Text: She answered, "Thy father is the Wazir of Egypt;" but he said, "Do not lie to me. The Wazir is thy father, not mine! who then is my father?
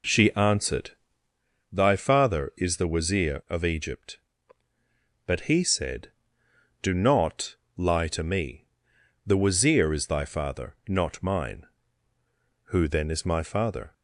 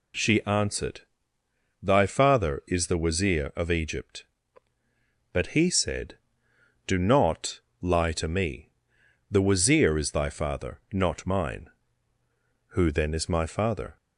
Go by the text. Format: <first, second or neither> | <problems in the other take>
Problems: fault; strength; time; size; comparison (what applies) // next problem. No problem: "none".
second | starts louder than the rest; noticeable; until 1.4 s; 4 dB // pauses between "not" and "lie"; slight; at 7.5 s; 0.20 s long; slight in the second